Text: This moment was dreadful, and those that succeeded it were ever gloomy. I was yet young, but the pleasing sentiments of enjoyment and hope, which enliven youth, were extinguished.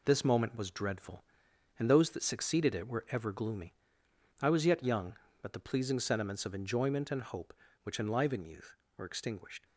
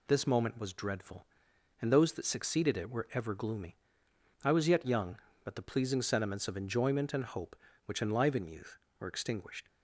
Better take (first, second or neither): second